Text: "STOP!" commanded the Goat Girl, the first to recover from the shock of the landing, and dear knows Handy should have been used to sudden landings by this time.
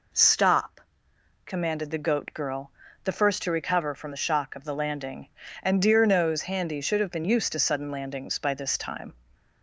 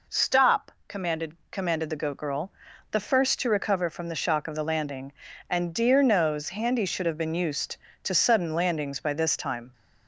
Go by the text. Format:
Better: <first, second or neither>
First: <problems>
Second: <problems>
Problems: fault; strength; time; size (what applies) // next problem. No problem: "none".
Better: first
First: none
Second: says "commanded" twice; at 1.5 s